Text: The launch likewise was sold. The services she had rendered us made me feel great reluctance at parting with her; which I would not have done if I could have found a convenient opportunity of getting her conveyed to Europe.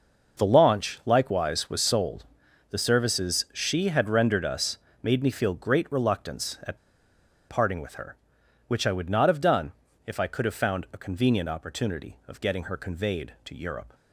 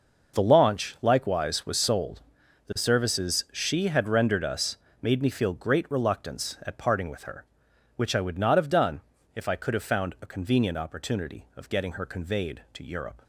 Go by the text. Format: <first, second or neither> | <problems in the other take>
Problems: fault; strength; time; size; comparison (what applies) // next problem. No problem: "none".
second | pauses between "us" and "made"; slight; at 4.7 s; 0.24 s long; slight in the second // pauses between "at" and "parting"; noticeable; at 6.7 s; 0.70 s long // pauses between "done" and "if"; slight; at 9.7 s; 0.32 s long; slight in the second